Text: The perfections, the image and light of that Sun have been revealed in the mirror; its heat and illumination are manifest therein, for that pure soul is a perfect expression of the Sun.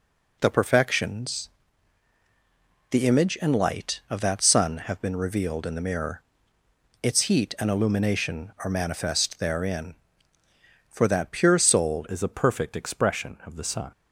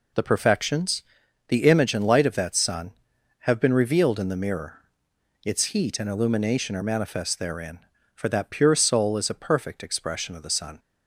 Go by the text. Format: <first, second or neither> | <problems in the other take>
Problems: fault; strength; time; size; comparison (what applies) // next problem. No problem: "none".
second | changes voice at "is"; from 12.0 s on; 1.9 s long